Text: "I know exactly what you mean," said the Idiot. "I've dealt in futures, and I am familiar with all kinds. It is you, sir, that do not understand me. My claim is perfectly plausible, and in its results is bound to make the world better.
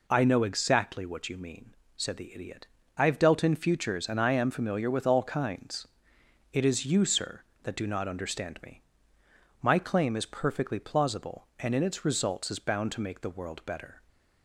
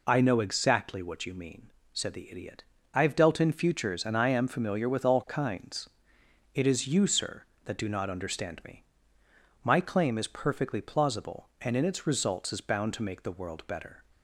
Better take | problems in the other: neither | none

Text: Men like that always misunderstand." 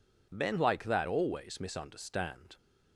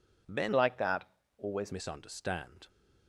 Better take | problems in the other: first | changes voice from "like" to "always"; from 0.5 to 1.7 s; 1.2 s long // pauses between "that" and "always"; slight; at 1.0 s; 0.32 s long

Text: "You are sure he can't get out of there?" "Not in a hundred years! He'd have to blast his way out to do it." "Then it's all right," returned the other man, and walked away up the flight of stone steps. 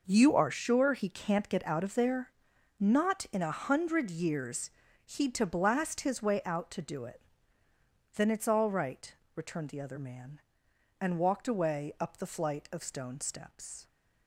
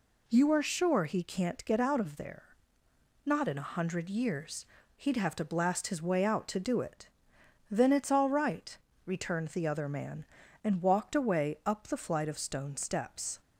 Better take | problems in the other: second | skips "have"; at 5.3 s

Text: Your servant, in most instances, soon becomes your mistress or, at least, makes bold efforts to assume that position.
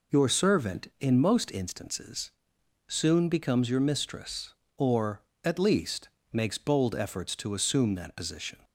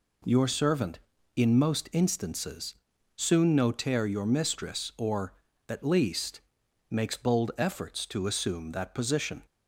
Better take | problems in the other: first | says "notaire" for "becomes"; at 3.5 s

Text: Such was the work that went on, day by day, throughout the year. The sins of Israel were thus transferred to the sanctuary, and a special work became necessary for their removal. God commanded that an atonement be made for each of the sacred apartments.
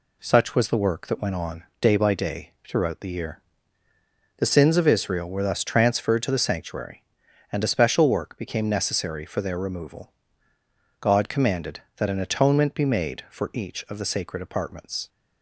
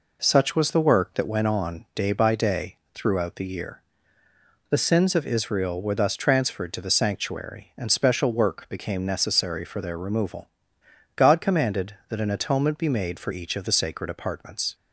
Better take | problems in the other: first | skips "a"; at 7.9 s

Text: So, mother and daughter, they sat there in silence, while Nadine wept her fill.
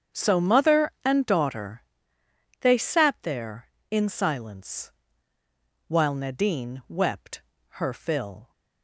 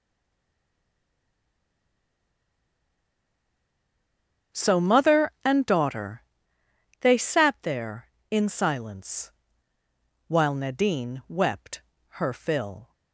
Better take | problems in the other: first | stays silent before the first word; strong; until 4.5 s; 4.5 s long // starts louder than the rest; strong; until 5.7 s; 7.5 dB; strong in the first // pauses between "wept" and "her"; slight; at 11.7 s; 0.36 s long; slight in the first

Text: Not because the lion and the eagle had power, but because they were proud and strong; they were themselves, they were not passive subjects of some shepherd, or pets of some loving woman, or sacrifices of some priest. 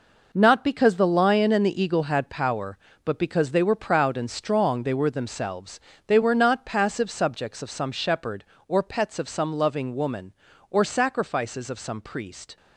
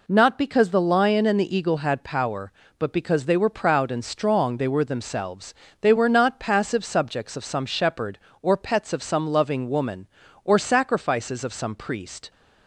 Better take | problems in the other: second | gets quieter; strong; throughout; 9 dB

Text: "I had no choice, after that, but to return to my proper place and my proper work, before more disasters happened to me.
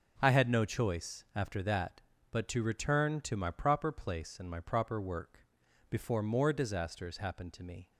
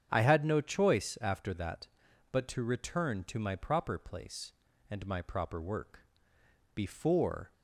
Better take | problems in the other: first | starts louder than the rest; strong; until 1.1 s; 8 dB // stops before "more disasters happened to me"; at 7.5 s

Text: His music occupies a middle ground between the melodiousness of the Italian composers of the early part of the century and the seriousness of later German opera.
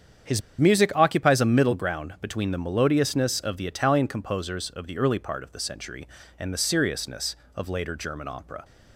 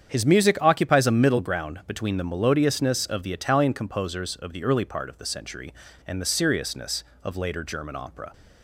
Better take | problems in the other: second | starts louder than the rest; strong; until 1.4 s; 8 dB; strong in the second // pauses between "His" and "music"; slight; at 0.4 s; 0.19 s long

